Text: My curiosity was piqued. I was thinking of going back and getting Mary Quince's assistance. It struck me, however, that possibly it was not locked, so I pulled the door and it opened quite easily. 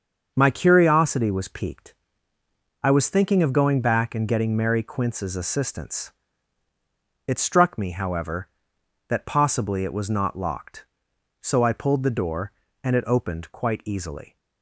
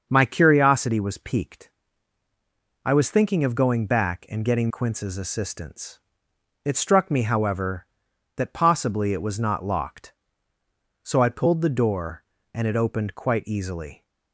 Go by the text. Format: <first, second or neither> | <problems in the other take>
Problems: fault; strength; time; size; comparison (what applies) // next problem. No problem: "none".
first | starts louder than the rest; until 1.1 s; 6.5 dB; also in the first // skips "Mary"; at 4.7 s